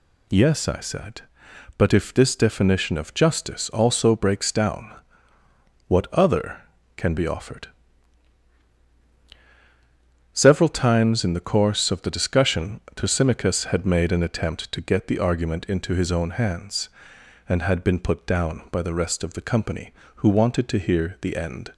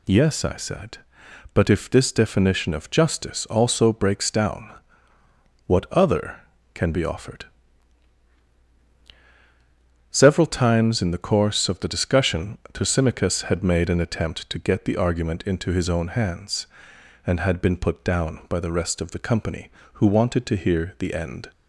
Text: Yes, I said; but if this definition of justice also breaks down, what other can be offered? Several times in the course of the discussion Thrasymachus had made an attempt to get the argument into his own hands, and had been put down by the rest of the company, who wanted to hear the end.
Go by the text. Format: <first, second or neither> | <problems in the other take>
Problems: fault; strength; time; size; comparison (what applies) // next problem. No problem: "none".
neither | pauses between "discussion" and "Thrasymachus"; slight; the same in both